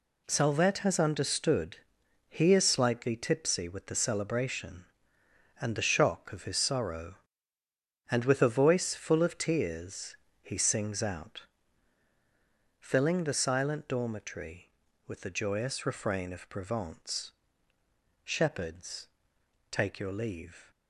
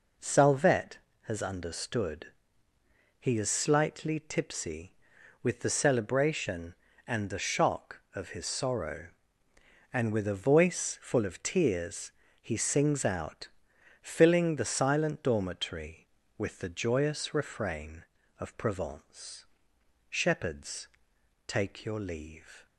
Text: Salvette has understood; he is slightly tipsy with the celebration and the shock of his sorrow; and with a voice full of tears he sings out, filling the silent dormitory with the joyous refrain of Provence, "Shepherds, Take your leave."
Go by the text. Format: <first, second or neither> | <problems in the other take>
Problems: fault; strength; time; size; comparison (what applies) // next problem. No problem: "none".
neither | pauses between "tears" and "he"; slight; the same in both